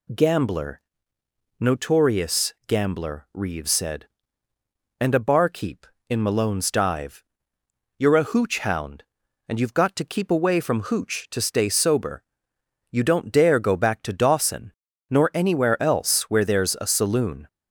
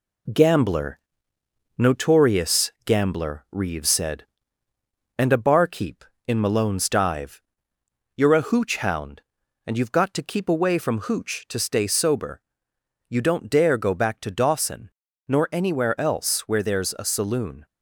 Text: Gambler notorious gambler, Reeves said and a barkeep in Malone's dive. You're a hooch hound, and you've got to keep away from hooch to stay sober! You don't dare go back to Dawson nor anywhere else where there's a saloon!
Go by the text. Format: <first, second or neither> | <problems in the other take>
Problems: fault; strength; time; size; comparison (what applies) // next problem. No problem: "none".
first | gets quieter; slight; throughout; 3 dB // pauses between "Gambler" and "notorious"; noticeable; at 0.9 s; 0.78 s long; noticeable in the first // pauses between "Dawson" and "nor"; at 14.8 s; 0.38 s long; also in the first